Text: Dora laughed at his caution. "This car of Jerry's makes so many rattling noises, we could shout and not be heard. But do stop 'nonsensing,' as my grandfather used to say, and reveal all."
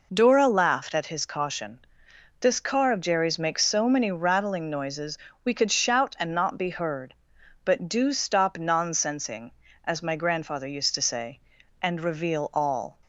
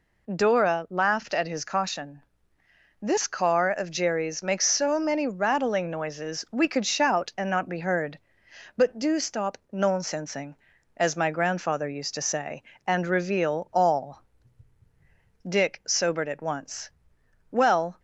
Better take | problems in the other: first | pauses between "stop" and "nonsensing"; slight; at 9.5 s; 0.16 s long // goes on to say "Dick sobered at once Well"; strong; from 15.4 s on; 2.5 s long

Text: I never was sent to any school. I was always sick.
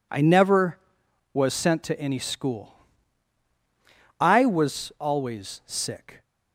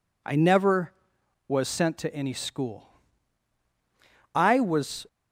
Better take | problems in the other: first | stops before "always sick"; at 5.0 s

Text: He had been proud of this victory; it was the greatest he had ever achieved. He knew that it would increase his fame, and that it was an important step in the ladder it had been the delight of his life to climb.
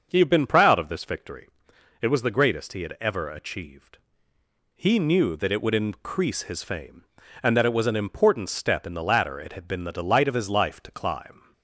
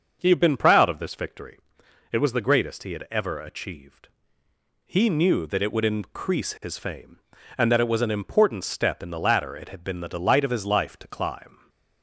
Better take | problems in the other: neither | starts louder than the rest; the same in both

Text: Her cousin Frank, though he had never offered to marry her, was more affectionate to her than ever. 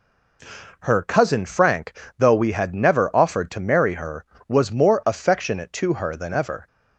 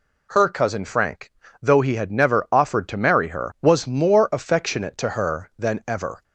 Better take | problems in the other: second | says "we" for "he"; at 2.3 s

